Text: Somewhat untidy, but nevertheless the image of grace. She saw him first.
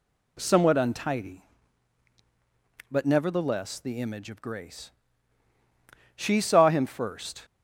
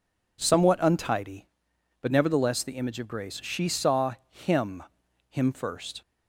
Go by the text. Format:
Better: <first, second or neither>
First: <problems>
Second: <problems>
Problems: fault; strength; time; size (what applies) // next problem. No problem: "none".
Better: first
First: none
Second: pauses between "saw" and "him"; slight; at 4.1 s; 0.16 s long // says "him" twice; at 5.2 s